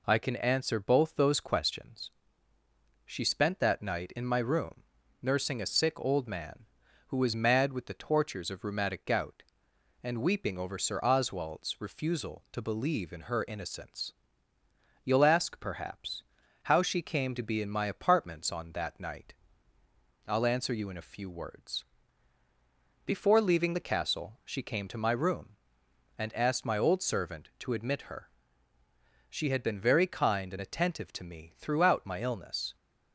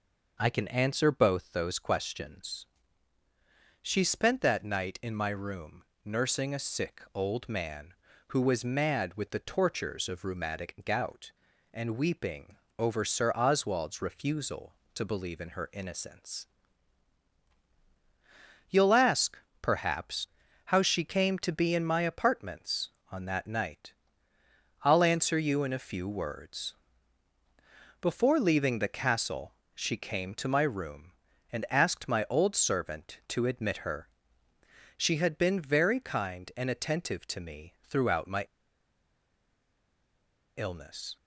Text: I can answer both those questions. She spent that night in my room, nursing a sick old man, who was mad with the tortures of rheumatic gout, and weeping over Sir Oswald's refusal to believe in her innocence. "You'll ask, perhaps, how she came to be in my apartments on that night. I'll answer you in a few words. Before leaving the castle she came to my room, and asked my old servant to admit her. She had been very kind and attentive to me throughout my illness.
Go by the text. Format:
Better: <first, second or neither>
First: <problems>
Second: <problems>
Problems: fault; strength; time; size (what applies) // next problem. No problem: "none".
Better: first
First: none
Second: pauses between "weeping" and "over"; slight; at 12.5 s; 0.22 s long // pauses between "castle" and "she"; slight; at 29.5 s; 0.20 s long // pauses between "my" and "illness"; strong; at 38.4 s; 2.1 s long